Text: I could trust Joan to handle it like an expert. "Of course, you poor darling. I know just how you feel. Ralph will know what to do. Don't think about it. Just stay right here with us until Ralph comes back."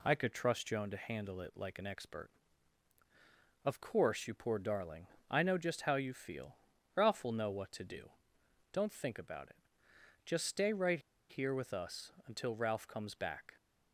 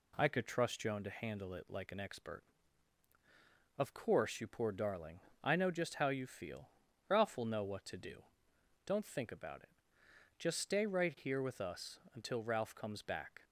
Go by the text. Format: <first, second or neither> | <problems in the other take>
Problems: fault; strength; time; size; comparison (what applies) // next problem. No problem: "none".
second | pauses between "right" and "here"; slight; at 10.9 s; 0.30 s long // pauses between "us" and "until"; slight; at 12.1 s; 0.16 s long; slight in the second